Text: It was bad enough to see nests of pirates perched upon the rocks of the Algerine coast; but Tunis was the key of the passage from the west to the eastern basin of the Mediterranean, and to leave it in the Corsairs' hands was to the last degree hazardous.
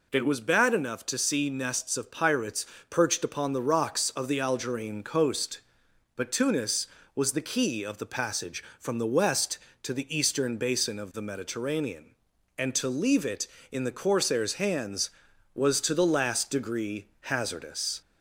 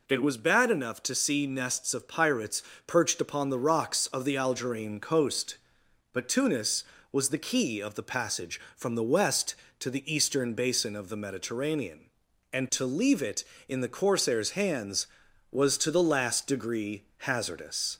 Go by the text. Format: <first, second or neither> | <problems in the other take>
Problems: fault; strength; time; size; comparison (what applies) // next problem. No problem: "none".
neither | pauses between "pirates" and "perched"; slight; the same in both